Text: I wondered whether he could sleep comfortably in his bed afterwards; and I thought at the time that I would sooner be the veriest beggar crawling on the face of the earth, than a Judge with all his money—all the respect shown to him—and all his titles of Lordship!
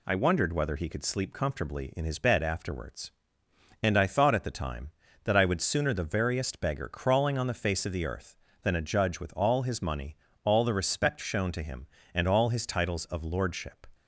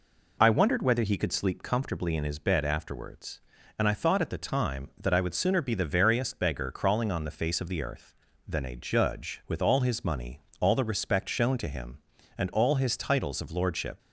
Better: second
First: skips "be"; at 5.9 s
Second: none

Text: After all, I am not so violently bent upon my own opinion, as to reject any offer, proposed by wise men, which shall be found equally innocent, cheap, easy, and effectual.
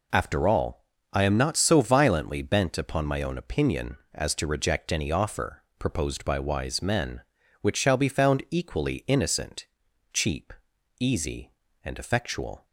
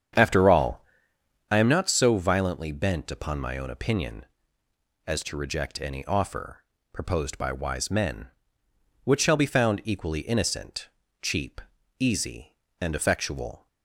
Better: first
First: none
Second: starts louder than the rest; strong; until 1.6 s; 8 dB

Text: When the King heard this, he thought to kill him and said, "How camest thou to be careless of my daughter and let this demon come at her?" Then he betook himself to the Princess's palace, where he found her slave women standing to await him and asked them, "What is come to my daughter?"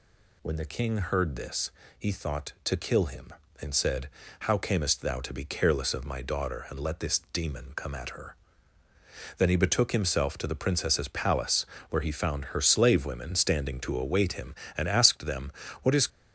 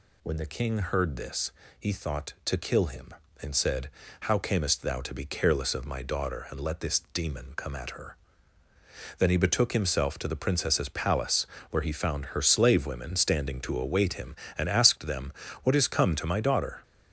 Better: second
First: stops before "come to my daughter"; at 16.0 s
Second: none

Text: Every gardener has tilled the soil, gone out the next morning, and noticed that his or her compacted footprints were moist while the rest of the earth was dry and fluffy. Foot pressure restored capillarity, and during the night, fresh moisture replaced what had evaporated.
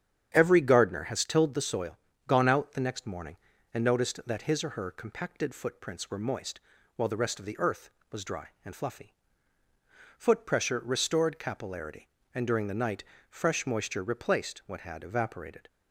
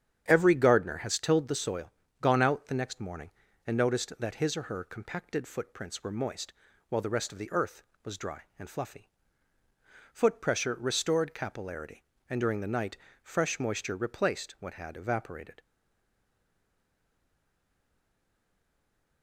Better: first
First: starts louder than the rest; strong; until 1.3 s; 9 dB // pauses between "moist" and "while"; slight; at 6.5 s; 0.36 s long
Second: starts louder than the rest; strong; until 1.2 s; 9 dB // pauses between "moist" and "while"; slight; at 6.5 s; 0.36 s long // stays silent after the last word; strong; from 15.5 s on; 3.7 s long

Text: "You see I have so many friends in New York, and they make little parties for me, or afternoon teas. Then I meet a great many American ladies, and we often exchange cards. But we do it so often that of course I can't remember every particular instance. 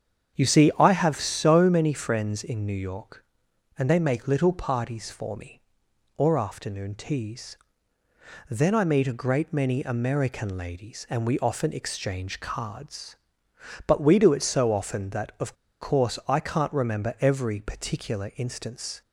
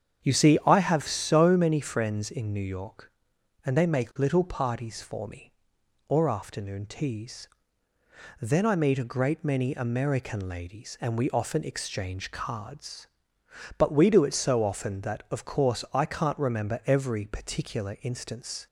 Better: second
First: starts louder than the rest; strong; until 1.4 s; 8 dB // pauses between "of" and "course"; slight; at 15.5 s; 0.25 s long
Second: starts louder than the rest; strong; until 1.2 s; 8 dB

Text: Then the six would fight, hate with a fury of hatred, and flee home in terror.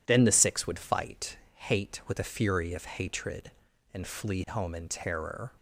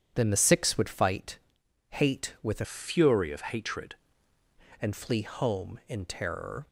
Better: first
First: none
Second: changes voice from "fury" to "hatred"; from 2.6 to 3.9 s; 1.3 s long

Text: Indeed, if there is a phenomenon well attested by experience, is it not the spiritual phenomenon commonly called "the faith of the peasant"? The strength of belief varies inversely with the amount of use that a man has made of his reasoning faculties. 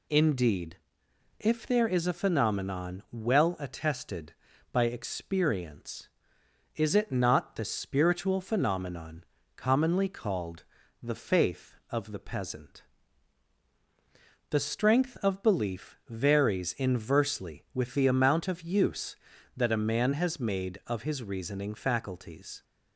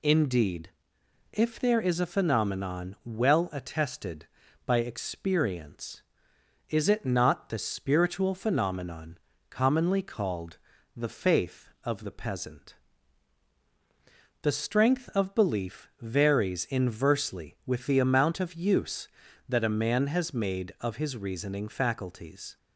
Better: neither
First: pauses between "phenomenon" and "commonly"; slight; at 9.2 s; 0.34 s long // pauses between "called" and "the"; at 10.6 s; 0.38 s long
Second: pauses between "phenomenon" and "commonly"; slight; at 9.1 s; 0.34 s long // pauses between "called" and "the"; at 10.5 s; 0.38 s long

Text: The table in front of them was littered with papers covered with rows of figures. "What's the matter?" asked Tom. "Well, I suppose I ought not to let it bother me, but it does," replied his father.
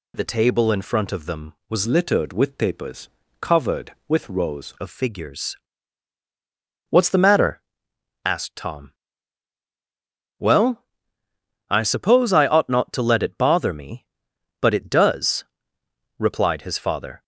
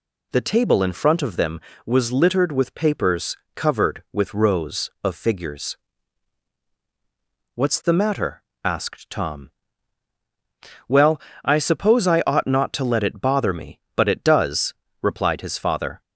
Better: second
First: changes voice from "littered" to "rows"; from 1.8 to 4.7 s; 2.9 s long // pauses between "papers" and "covered"; slight; at 3.0 s; 0.32 s long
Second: pauses between "papers" and "covered"; slight; at 3.3 s; 0.20 s long

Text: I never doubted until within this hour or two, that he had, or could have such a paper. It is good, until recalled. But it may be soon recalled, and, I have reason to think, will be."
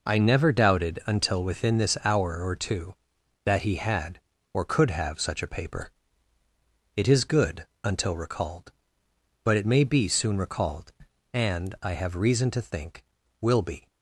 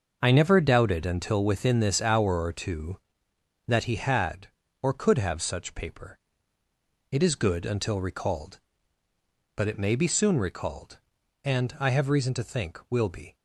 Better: first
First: none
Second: starts louder than the rest; noticeable; until 1.2 s; 6 dB // skips "a"; at 5.7 s

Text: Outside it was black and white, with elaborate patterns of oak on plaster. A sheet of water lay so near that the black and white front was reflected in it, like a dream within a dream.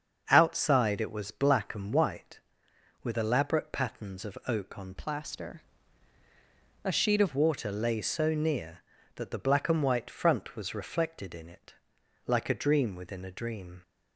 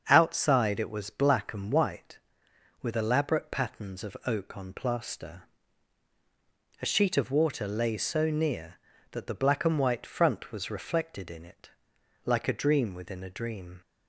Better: second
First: starts louder than the rest; until 1.3 s; 7 dB // changes voice from "plaster" to "of"; from 4.9 to 7.3 s; 2.4 s long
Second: starts louder than the rest; until 1.0 s; 7 dB

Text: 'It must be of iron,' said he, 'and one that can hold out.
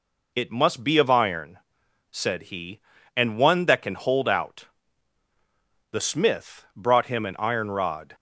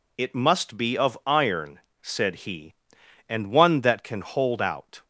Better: second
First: goes on to say "The smith brought him an iron rod"; strong; from 5.9 s on; 2.2 s long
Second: none

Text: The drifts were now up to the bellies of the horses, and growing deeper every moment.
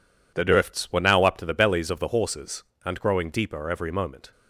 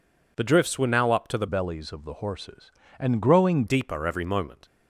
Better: first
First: none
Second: changes voice from "bellies" to "growing"; from 1.4 to 3.6 s; 2.2 s long

